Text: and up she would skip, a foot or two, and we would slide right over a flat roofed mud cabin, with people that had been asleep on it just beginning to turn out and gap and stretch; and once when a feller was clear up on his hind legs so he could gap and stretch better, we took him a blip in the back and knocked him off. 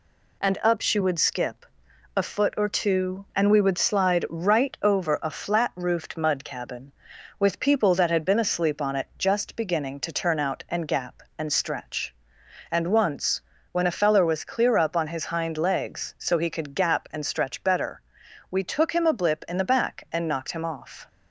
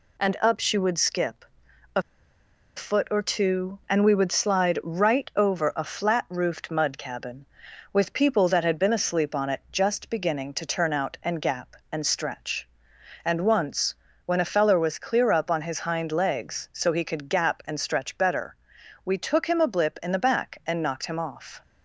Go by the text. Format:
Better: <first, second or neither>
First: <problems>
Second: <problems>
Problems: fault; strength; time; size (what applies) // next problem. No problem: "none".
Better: first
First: pauses between "once" and "when"; slight; at 13.3 s; 0.30 s long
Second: pauses between "a" and "foot"; noticeable; at 2.0 s; 0.75 s long // pauses between "once" and "when"; slight; at 13.9 s; 0.30 s long